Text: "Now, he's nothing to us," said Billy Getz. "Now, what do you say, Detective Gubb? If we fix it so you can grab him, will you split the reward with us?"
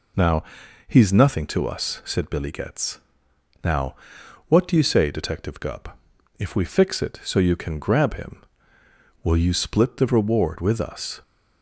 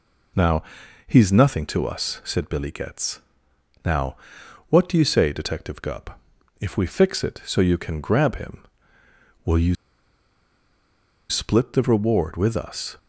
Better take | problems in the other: first | pauses between "you" and "split"; strong; at 9.7 s; 1.5 s long

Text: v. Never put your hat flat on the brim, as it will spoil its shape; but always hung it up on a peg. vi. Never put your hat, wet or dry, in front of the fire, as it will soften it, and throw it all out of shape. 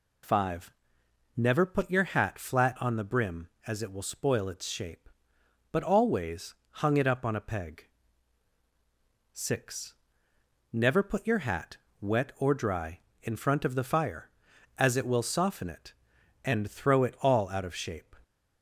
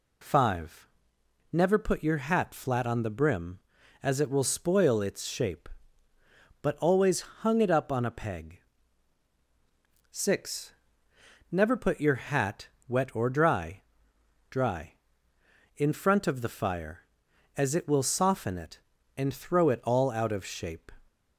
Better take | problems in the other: first | pauses between "always" and "hung"; slight; at 7.2 s; 0.22 s long; slight in the first // says "dry" twice; at 14.5 s

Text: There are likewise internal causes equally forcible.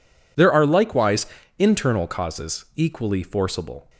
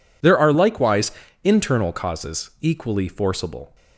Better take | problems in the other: neither | pauses between "likewise" and "internal"; slight; the same in both

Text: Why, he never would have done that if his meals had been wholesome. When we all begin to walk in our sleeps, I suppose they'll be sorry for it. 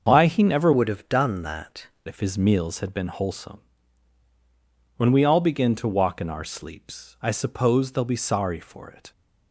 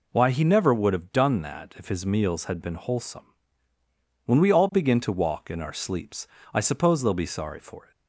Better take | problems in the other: second | starts louder than the rest; until 1.1 s; 6.5 dB // changes voice from "would" to "that"; from 0.7 to 1.8 s; 1.1 s long

